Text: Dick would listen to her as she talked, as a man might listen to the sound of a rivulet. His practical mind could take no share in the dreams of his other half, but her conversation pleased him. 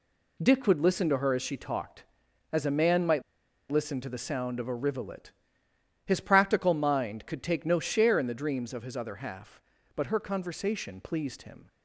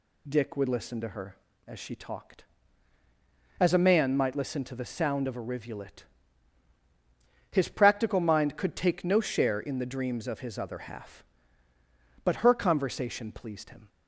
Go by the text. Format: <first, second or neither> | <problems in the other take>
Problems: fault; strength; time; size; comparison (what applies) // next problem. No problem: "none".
second | pauses between "might" and "listen"; noticeable; at 3.2 s; 0.49 s long